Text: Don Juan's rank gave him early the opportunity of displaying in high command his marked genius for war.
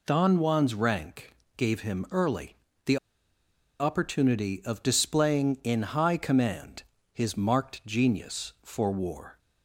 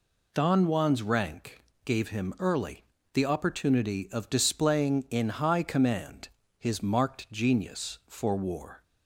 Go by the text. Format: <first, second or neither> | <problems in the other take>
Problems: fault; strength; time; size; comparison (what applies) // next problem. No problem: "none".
second | pauses between "rank" and "gave"; slight; at 1.3 s; 0.22 s long; slight in the second // pauses between "early" and "the"; slight; at 2.5 s; 0.30 s long; slight in the second // pauses between "the" and "opportunity"; noticeable; at 2.9 s; 0.83 s long // pauses between "command" and "his"; slight; at 6.8 s; 0.32 s long; slight in the second